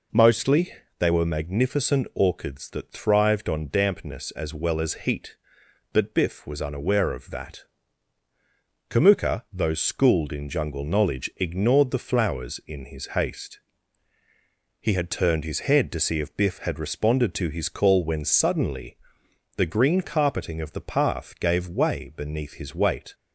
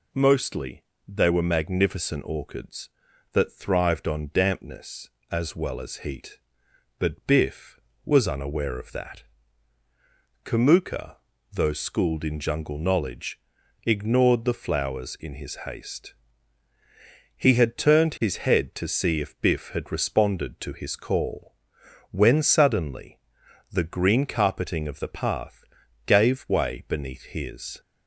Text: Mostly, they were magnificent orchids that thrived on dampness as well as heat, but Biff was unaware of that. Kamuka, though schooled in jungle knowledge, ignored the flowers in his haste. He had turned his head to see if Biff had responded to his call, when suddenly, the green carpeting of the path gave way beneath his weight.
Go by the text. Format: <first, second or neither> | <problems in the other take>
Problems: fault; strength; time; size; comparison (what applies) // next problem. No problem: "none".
first | pauses between "path" and "gave"; at 25.6 s; 0.42 s long // stops before "weight"; at 27.7 s